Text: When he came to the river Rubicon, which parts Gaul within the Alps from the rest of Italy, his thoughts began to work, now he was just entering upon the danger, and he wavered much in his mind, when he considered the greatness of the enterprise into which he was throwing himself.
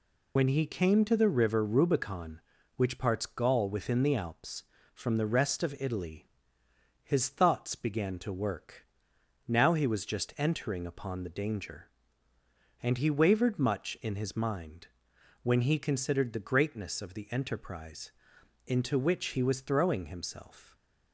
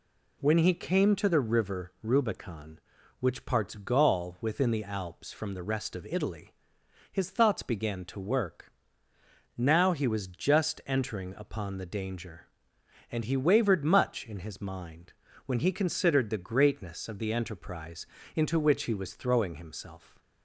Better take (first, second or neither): second